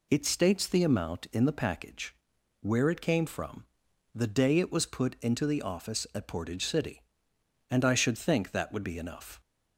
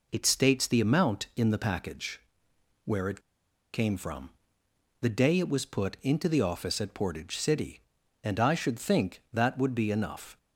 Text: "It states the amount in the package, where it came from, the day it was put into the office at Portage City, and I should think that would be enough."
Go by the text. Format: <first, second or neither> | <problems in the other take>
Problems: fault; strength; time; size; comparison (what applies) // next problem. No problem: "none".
first | pauses between "it" and "came"; noticeable; at 3.1 s; 0.54 s long